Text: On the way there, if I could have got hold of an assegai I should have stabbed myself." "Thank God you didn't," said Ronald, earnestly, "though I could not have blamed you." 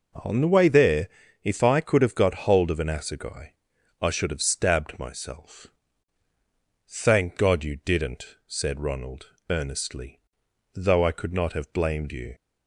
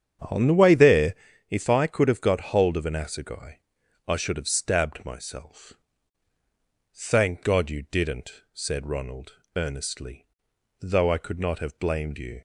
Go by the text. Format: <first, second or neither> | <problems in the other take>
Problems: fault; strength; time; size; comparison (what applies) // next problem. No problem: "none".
first | starts louder than the rest; strong; until 1.3 s; 8.5 dB // pauses between "assegai" and "I"; noticeable; at 3.5 s; 0.48 s long; noticeable in the first